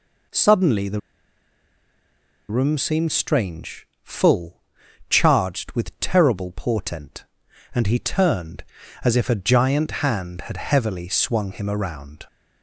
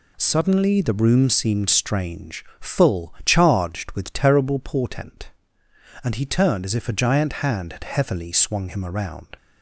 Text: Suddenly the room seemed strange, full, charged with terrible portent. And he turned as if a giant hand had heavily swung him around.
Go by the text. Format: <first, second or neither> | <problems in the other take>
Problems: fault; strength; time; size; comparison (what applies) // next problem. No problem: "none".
second | pauses between "the" and "room"; strong; at 0.9 s; 1.4 s long